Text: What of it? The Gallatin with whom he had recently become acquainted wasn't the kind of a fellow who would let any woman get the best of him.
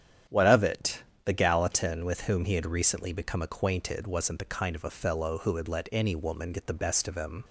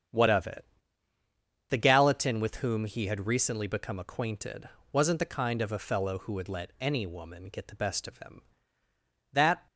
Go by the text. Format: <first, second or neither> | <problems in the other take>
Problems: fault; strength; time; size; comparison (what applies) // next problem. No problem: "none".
first | starts louder than the rest; strong; until 2.1 s; 8 dB; strong in the first // pauses between "acquainted" and "wasn't"; slight; at 4.6 s; 0.24 s long // goes on to say "That"; slight; from 9.3 s on; 0.34 s long